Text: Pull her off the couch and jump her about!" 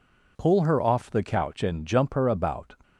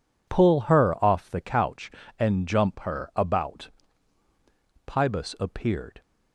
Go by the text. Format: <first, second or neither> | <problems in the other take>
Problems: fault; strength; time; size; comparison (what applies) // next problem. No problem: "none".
first | goes on to say "Pybus appeared"; noticeable; from 4.8 s on; 1.1 s long